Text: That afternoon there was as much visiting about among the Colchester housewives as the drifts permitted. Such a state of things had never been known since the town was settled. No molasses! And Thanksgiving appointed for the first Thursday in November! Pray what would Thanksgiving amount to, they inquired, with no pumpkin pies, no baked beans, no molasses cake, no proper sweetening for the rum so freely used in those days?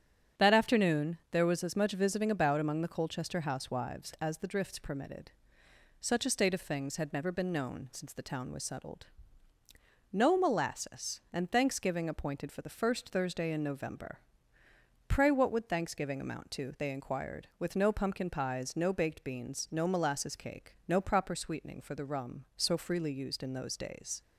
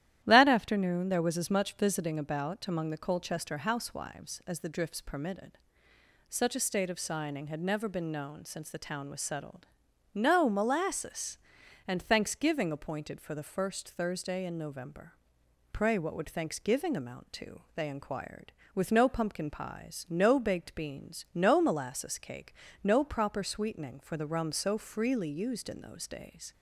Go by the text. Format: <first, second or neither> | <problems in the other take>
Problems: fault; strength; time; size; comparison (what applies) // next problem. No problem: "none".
first | starts louder than the rest; strong; until 1.2 s; 12.5 dB; strong in the first // says "signing" for "things"; at 6.9 s